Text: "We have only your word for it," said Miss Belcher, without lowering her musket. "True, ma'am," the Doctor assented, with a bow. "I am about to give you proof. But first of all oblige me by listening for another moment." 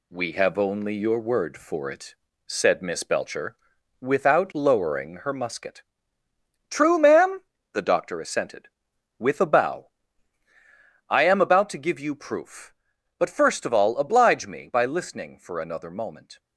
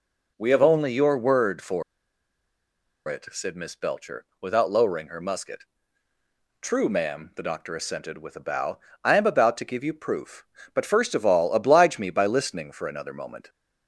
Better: first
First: none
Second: pauses between "for" and "it"; strong; at 1.8 s; 1.2 s long

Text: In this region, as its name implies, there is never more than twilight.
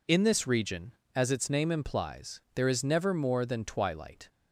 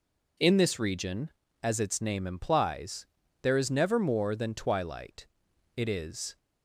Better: first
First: none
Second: goes on to say "It is"; noticeable; from 5.7 s on; 0.62 s long

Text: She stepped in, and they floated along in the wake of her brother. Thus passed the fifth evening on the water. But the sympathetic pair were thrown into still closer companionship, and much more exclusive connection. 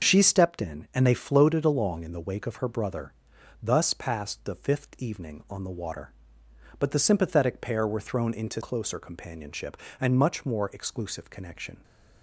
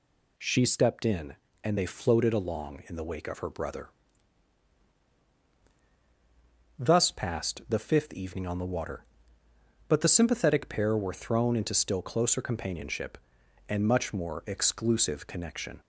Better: second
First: skips "still"; at 8.6 s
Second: none

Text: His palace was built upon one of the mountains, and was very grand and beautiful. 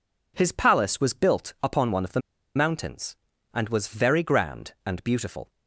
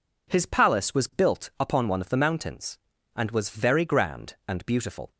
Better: second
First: pauses between "the" and "mountains"; at 2.1 s; 0.36 s long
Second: none

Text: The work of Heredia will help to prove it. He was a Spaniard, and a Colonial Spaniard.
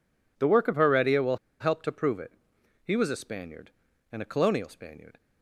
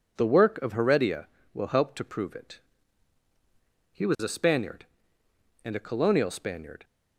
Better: second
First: pauses between "will" and "help"; slight; at 1.3 s; 0.22 s long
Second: none

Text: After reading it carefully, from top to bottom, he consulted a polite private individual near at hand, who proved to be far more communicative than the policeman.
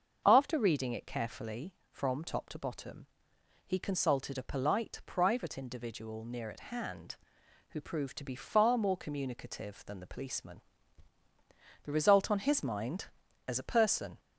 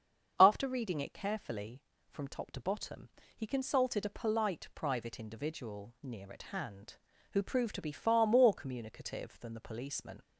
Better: second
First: starts louder than the rest; until 1.2 s; 6.5 dB // goes on to say "The result on his mind as a person"; strong; from 11.8 s on; 2.3 s long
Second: starts louder than the rest; until 1.3 s; 7 dB

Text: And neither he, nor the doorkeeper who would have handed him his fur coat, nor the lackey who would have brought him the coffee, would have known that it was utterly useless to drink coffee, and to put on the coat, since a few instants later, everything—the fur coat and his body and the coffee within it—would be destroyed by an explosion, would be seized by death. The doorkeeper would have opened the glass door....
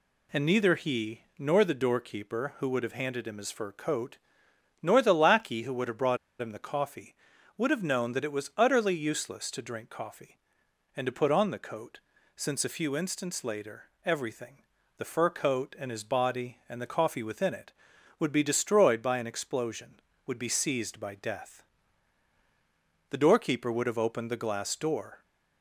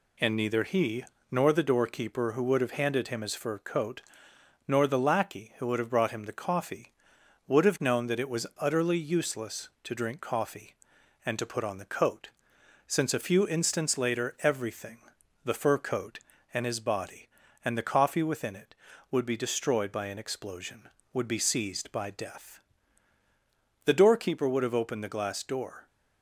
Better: second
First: pauses between "brought" and "him"; slight; at 6.1 s; 0.24 s long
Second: none

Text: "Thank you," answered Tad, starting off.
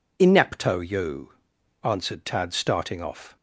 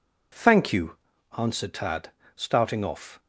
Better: second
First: says "Inepto" for "Thank"; at 0.2 s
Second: none

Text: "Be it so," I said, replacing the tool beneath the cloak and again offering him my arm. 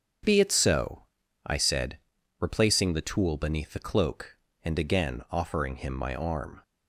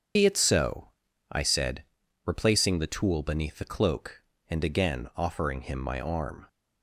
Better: first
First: starts louder than the rest; strong; until 1.6 s; 7.5 dB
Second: loses the start of "Be"; at 0.1 s; 65 ms // starts louder than the rest; strong; until 1.5 s; 7.5 dB

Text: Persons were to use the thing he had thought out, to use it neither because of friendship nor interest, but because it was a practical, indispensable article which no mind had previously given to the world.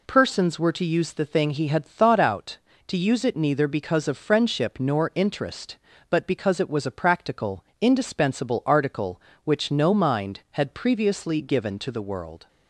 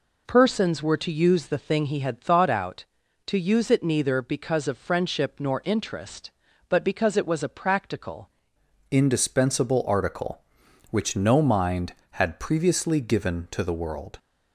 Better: first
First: none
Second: changes voice at "indispensable"; from 8.8 s on; 5.3 s long

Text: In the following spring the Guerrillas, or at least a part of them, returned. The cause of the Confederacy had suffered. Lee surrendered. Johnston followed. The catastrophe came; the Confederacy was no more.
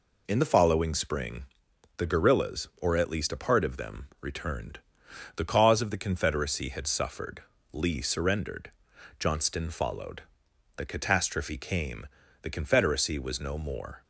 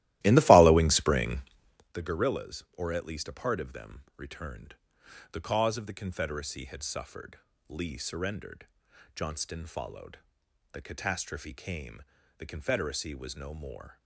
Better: first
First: pauses between "spring" and "the"; noticeable; at 1.4 s; 0.52 s long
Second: starts louder than the rest; strong; until 2.0 s; 16 dB // pauses between "spring" and "the"; noticeable; at 1.4 s; 0.52 s long

